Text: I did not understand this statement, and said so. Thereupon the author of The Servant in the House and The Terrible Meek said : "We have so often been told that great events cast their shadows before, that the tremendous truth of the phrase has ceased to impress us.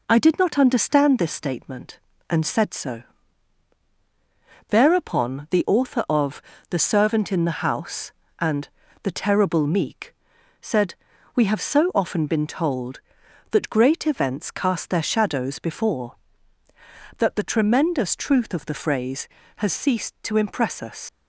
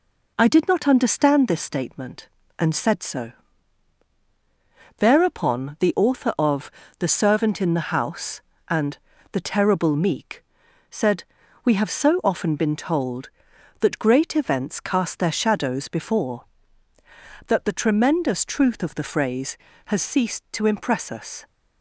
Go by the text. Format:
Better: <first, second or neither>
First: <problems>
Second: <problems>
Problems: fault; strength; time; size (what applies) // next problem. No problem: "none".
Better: second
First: pauses between "of" and "The"; slight; at 6.4 s; 0.26 s long // pauses between "and" and "The"; slight; at 8.6 s; 0.32 s long // pauses between "Meek" and "said"; noticeable; at 10.1 s; 0.48 s long // leaves "us" unfinished; at 21.0 s; 80 ms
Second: pauses between "of" and "The"; slight; at 6.7 s; 0.26 s long // pauses between "and" and "The"; slight; at 8.9 s; 0.32 s long // pauses between "Meek" and "said"; noticeable; at 10.4 s; 0.48 s long